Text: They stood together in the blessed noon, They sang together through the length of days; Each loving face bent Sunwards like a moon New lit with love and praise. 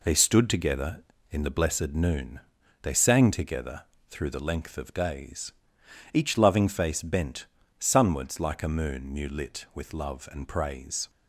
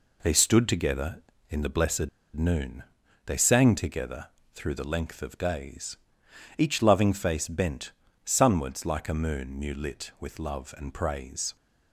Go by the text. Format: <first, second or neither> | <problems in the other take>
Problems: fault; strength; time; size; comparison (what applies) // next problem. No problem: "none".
first | pauses between "blessed" and "noon"; slight; at 2.0 s; 0.26 s long // pauses between "together" and "through"; slight; at 4.2 s; 0.26 s long; slight in the first // pauses between "bent" and "Sunwards"; slight; at 7.9 s; 0.32 s long; slight in the first